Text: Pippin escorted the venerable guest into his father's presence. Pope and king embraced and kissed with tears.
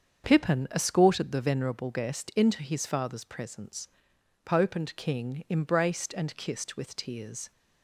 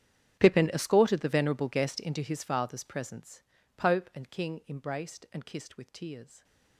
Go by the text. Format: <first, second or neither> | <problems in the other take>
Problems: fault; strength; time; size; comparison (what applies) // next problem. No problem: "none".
first | gets quieter; strong; throughout; 21 dB // starts louder than the rest; strong; until 1.4 s; 9.5 dB; strong in the first